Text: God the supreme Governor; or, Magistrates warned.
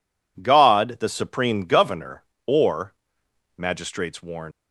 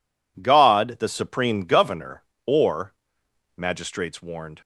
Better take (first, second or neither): second